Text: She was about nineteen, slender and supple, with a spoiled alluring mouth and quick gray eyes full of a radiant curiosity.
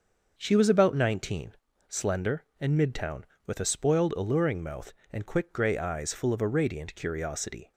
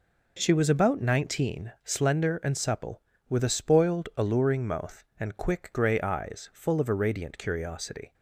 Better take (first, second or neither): second